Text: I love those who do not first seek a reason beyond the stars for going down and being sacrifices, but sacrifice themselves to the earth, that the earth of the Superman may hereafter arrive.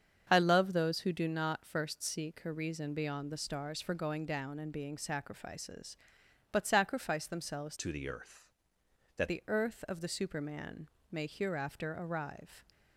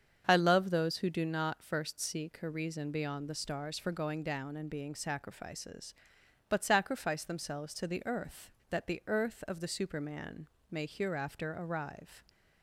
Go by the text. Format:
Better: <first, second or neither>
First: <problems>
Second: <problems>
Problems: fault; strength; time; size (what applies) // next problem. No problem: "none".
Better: second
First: starts louder than the rest; strong; until 1.3 s; 7 dB // changes voice from "to" to "that"; from 7.7 to 9.2 s; 1.5 s long // pauses between "Superman" and "may"; slight; at 10.8 s; 0.22 s long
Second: starts louder than the rest; strong; until 1.3 s; 7 dB // pauses between "Superman" and "may"; slight; at 10.4 s; 0.22 s long